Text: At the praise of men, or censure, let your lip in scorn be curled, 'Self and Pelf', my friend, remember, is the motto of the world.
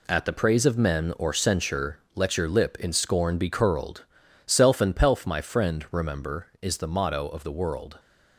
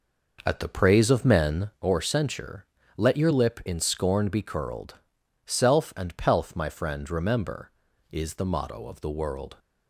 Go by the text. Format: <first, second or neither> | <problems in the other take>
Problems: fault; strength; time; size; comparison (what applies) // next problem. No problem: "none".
first | starts louder than the rest; noticeable; until 1.8 s; 5.5 dB